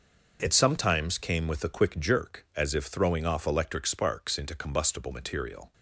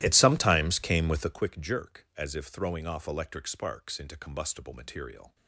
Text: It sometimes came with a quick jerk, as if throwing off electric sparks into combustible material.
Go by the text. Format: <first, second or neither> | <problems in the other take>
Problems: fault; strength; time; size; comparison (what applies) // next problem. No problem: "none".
first | starts louder than the rest; strong; until 1.4 s; 14.5 dB